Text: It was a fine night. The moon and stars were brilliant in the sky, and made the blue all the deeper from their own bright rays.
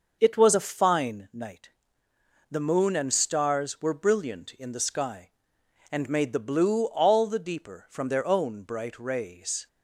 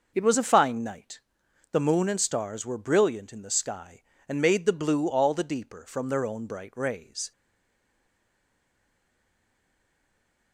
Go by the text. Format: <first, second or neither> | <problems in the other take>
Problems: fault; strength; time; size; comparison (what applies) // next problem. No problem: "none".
first | stays silent after the last word; strong; from 7.3 s on; 3.2 s long